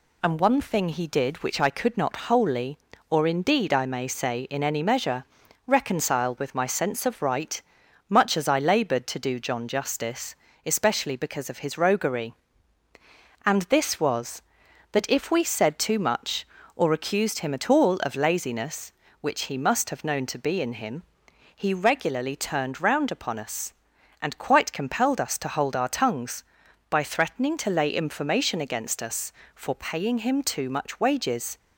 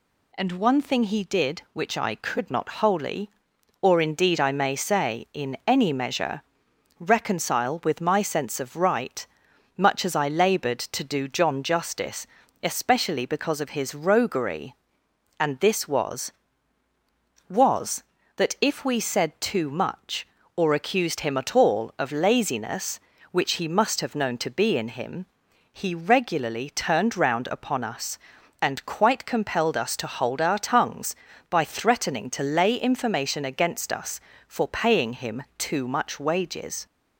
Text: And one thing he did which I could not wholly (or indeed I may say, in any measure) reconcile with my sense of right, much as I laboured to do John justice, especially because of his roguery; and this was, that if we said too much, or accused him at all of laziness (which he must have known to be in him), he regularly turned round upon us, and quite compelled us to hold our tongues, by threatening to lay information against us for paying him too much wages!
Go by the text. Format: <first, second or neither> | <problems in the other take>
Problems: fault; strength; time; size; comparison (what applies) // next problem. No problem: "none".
first | says "was" twice; at 17.4 s // pauses between "him" and "too"; slight; at 35.4 s; 0.16 s long